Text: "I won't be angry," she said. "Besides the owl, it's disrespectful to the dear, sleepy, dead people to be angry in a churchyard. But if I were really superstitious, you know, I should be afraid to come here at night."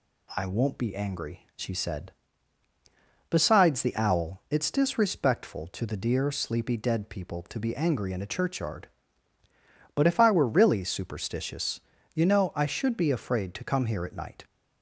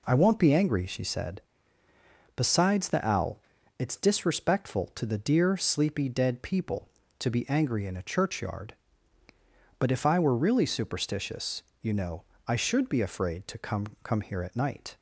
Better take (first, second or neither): first